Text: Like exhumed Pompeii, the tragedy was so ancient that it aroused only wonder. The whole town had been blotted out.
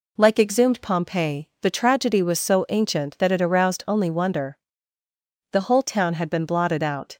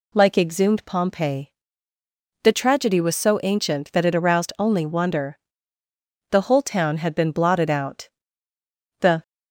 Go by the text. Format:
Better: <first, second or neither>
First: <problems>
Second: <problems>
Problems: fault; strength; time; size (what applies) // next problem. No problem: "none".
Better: first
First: none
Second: goes on to say "The"; slight; from 9.0 s on; 0.22 s long